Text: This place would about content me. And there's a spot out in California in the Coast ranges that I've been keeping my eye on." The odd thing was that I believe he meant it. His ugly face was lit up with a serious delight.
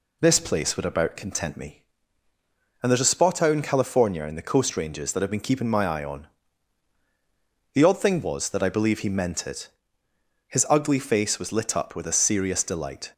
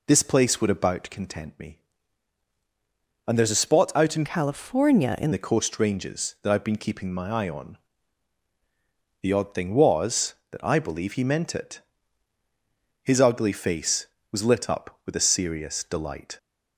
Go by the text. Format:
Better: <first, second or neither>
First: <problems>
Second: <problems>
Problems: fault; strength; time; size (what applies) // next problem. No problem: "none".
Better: first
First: none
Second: changes voice from "California" to "in"; from 4.2 to 5.3 s; 1.1 s long